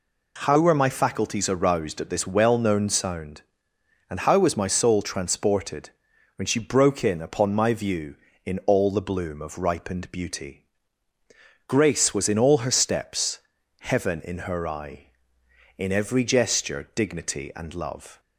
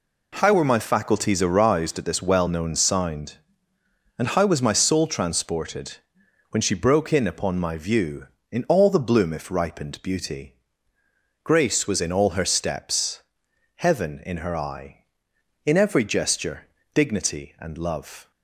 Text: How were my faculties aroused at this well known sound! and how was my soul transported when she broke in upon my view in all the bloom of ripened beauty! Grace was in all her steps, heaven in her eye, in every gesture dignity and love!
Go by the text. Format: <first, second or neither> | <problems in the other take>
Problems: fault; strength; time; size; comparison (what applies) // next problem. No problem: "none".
first | pauses between "transported" and "when"; noticeable; at 5.9 s; 0.54 s long; noticeable in the first // says "if" for "of"; at 9.3 s // pauses between "gesture" and "dignity"; slight; at 16.6 s; 0.30 s long